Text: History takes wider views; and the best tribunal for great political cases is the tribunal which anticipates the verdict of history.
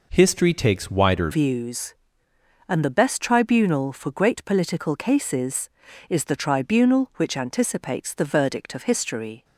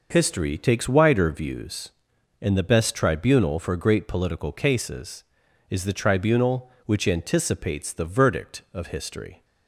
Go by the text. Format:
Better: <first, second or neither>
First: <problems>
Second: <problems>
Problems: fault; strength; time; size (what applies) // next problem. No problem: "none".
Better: second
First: changes voice at "views"; from 1.3 s on; 8.1 s long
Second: none